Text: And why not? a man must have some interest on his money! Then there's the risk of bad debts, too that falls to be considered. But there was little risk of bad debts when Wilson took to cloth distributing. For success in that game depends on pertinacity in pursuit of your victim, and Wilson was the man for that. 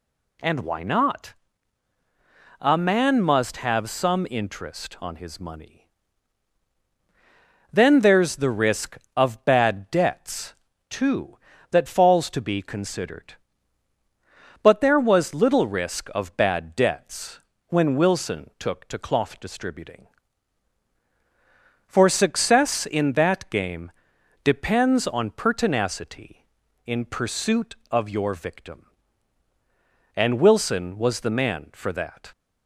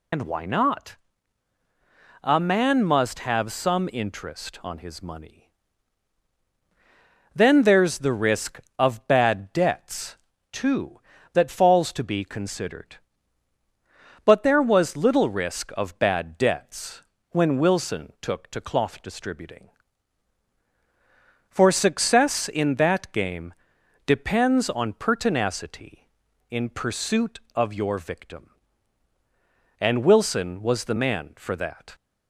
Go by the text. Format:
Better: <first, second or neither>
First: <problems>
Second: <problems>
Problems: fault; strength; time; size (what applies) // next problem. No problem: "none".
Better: first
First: pauses between "debts" and "when"; slight; at 17.3 s; 0.28 s long // pauses between "game" and "depends"; noticeable; at 23.9 s; 0.52 s long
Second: loses the start of "And"; at 0.1 s; 90 ms // pauses between "debts" and "when"; slight; at 17.0 s; 0.28 s long // pauses between "game" and "depends"; noticeable; at 23.5 s; 0.52 s long